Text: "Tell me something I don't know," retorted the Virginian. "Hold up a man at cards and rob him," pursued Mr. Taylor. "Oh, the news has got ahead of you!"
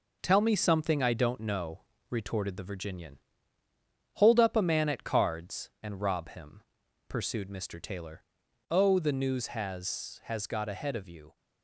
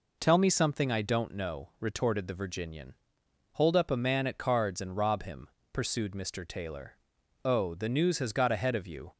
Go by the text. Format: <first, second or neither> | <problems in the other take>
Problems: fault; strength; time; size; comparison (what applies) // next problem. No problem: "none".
second | says "has" twice; at 10.2 s